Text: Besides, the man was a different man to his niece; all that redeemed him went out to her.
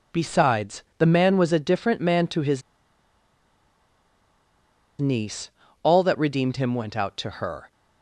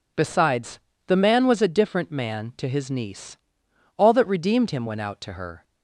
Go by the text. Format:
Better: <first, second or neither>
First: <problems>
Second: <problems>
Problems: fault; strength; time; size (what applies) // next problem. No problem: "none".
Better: second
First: pauses between "his" and "niece"; strong; at 2.6 s; 2.3 s long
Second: none